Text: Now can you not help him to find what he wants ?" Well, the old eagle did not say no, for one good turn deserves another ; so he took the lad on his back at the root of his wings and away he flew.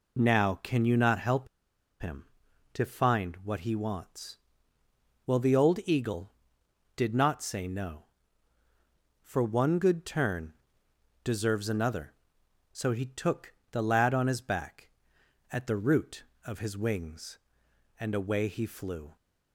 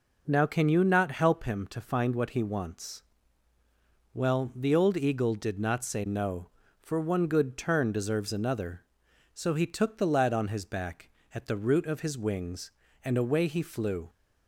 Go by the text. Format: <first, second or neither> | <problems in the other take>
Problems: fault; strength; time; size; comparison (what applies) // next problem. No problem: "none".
second | pauses between "help" and "him"; noticeable; at 1.4 s; 0.54 s long // pauses between "turn" and "deserves"; noticeable; at 10.5 s; 0.70 s long // pauses between "took" and "the"; slight; at 13.5 s; 0.20 s long